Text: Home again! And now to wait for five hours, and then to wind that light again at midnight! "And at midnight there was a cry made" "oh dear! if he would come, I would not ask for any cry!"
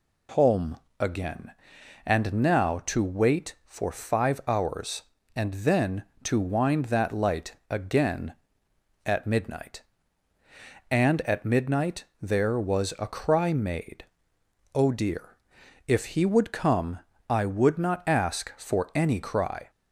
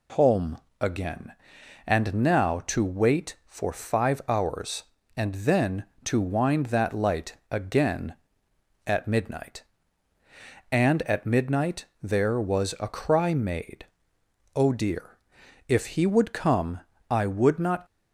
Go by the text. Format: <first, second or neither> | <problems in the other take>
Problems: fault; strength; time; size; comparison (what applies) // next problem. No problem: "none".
first | pauses between "Home" and "again"; slight; at 0.5 s; 0.24 s long; slight in the first // pauses between "midnight" and "there"; slight; at 11.8 s; 0.18 s long; slight in the first // pauses between "made" and "oh"; noticeable; at 13.8 s; 0.68 s long; noticeable in the first // stops before "ask for any cry"; at 17.8 s